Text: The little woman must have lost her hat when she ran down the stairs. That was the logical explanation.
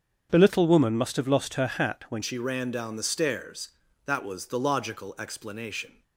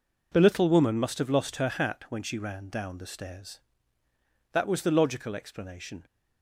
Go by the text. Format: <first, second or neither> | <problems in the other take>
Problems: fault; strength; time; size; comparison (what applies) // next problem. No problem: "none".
second | starts louder than the rest; strong; until 1.3 s; 7.5 dB // changes voice at "she"; from 2.2 s on; 3.8 s long